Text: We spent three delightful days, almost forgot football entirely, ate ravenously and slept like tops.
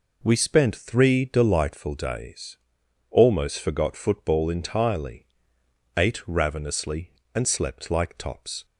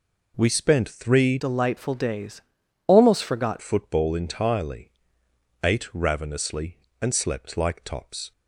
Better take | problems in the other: first | changes voice from "delightful" to "forgot"; from 1.3 to 3.5 s; 2.2 s long

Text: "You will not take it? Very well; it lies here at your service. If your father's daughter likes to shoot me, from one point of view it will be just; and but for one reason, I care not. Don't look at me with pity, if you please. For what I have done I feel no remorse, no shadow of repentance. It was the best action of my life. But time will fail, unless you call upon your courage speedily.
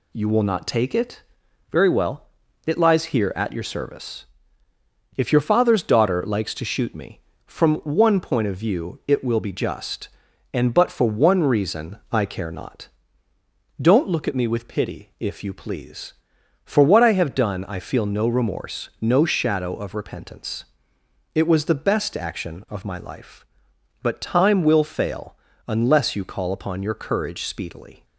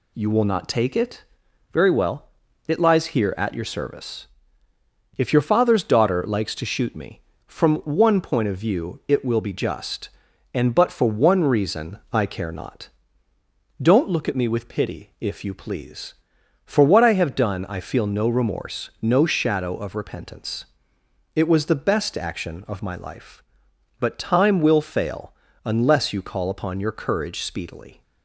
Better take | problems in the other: neither | none

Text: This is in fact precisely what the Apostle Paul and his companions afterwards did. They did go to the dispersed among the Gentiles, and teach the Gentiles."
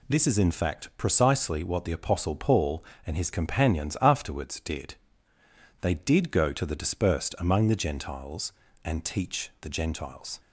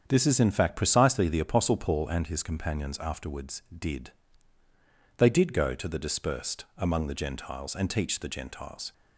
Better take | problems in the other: first | starts louder than the rest; strong; until 1.0 s; 7.5 dB // skips "what"; at 1.2 s

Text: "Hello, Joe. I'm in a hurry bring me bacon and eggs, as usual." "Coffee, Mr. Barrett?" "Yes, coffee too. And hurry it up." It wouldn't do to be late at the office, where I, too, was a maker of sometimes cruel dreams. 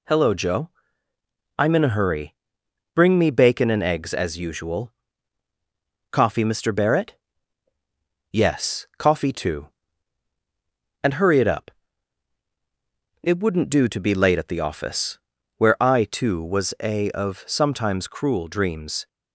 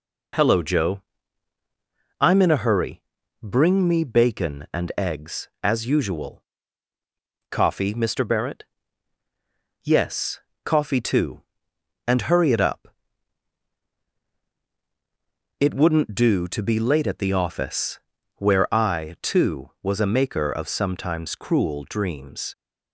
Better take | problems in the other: second | pauses between "hurry" and "bring"; noticeable; at 2.3 s; 0.58 s long; also in the second // skips "maker"; at 17.0 s

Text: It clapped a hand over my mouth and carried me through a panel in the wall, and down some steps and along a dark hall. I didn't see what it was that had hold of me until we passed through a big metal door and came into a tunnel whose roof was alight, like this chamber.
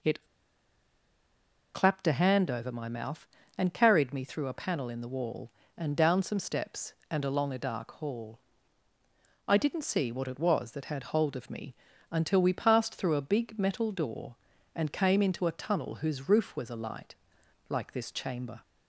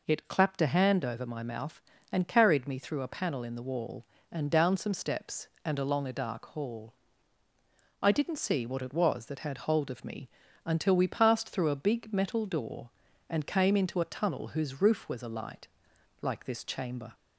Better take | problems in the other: second | pauses between "It" and "clapped"; strong; at 0.2 s; 1.4 s long // pauses between "me" and "until"; slight; at 11.7 s; 0.36 s long; slight in the second

